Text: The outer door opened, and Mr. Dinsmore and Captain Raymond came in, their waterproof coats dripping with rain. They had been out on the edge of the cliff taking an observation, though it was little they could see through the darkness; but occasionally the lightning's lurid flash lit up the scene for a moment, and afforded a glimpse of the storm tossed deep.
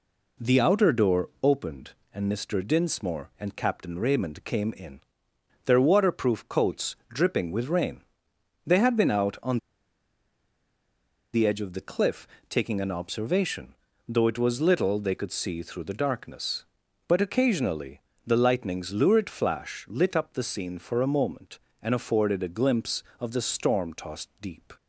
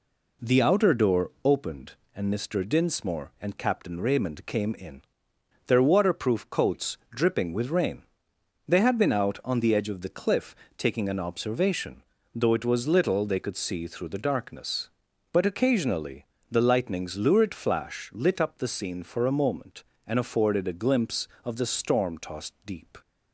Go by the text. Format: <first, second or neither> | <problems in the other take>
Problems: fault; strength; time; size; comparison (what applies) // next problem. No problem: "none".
second | pauses between "on" and "the"; strong; at 9.5 s; 1.7 s long // pauses between "cliff" and "taking"; slight; at 12.2 s; 0.22 s long; slight in the second // pauses between "occasionally" and "the"; slight; at 18.0 s; 0.24 s long; slight in the second